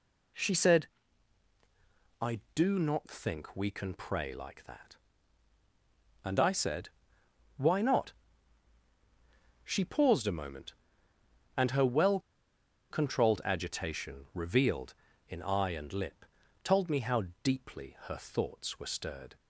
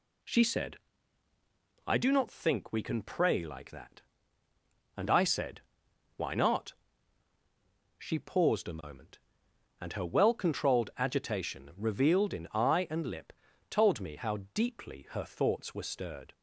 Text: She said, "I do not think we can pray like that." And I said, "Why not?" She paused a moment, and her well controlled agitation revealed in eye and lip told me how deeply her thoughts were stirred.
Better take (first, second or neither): second